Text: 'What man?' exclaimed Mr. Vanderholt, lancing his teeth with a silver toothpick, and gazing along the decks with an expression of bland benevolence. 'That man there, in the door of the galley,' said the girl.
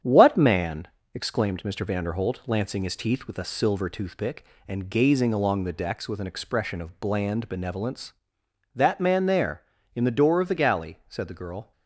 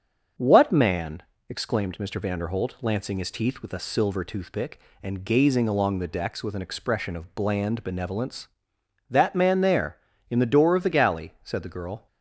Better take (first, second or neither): second